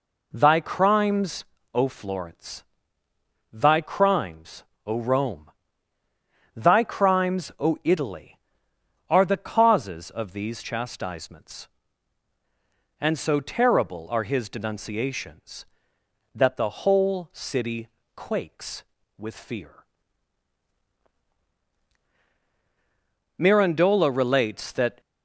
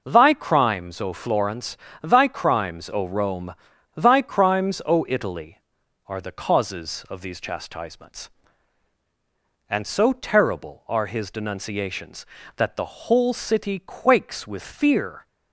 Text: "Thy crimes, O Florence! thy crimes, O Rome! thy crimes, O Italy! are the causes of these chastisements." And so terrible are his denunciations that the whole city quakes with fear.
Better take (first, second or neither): second